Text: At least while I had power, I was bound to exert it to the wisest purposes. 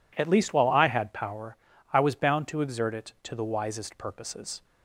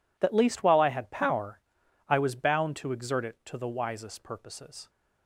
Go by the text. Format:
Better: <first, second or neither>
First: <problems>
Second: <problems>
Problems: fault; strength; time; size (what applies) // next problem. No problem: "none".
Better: first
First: none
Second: says "That" for "At"; at 0.1 s